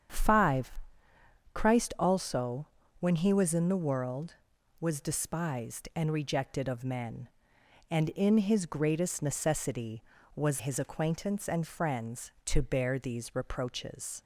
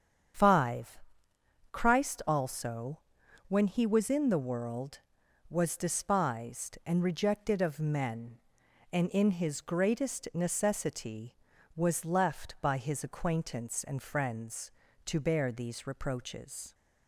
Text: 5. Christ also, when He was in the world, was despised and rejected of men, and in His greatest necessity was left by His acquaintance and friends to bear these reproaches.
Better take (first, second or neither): second